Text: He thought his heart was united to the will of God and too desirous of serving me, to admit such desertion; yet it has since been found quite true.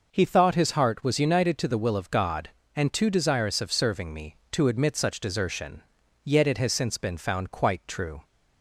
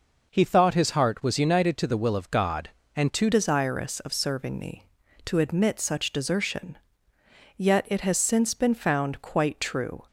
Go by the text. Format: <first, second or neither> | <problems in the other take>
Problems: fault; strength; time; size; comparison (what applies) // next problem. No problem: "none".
first | changes voice at "desirous"; from 3.3 s on; 6.7 s long